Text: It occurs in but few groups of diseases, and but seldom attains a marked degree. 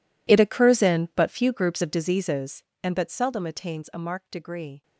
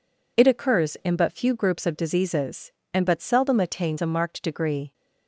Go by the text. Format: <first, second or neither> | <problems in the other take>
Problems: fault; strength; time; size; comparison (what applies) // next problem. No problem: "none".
second | gets quieter; strong; throughout; 20.5 dB